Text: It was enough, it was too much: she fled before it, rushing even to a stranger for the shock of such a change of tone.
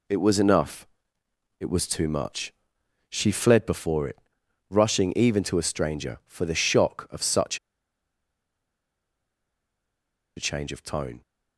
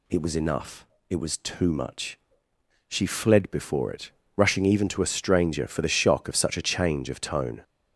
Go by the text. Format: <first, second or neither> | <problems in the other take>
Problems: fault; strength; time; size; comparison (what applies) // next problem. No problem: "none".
second | pauses between "such" and "a"; strong; at 7.5 s; 2.7 s long